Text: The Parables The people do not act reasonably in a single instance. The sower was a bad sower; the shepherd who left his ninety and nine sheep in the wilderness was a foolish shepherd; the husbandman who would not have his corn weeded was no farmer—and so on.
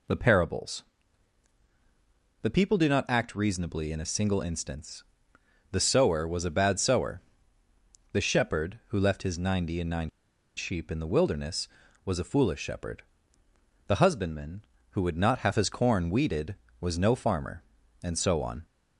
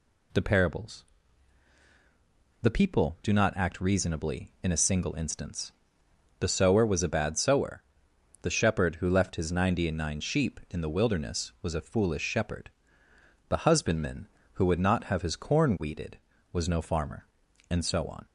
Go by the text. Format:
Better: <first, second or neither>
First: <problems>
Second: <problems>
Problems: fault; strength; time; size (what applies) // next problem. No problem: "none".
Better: second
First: pauses between "Parables" and "The"; strong; at 0.8 s; 1.6 s long // pauses between "nine" and "sheep"; noticeable; at 10.0 s; 0.47 s long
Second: pauses between "Parables" and "The"; strong; at 1.0 s; 1.5 s long